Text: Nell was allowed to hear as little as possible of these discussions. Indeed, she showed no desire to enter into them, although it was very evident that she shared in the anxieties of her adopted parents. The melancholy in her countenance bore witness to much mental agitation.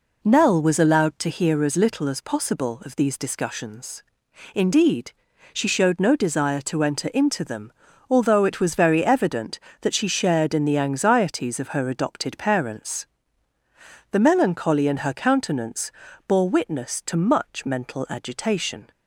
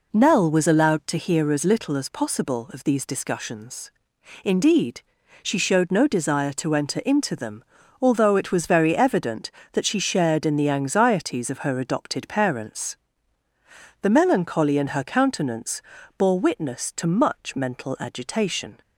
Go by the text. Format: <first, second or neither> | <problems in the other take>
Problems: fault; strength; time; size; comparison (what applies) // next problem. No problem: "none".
neither | pauses between "countenance" and "bore"; slight; the same in both